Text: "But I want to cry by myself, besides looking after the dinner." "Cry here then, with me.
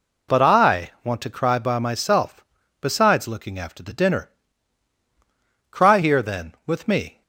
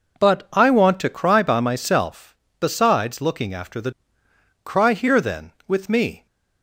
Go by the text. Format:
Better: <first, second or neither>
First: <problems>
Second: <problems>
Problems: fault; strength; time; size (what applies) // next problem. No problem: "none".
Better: first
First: none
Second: skips "dinner"; at 4.2 s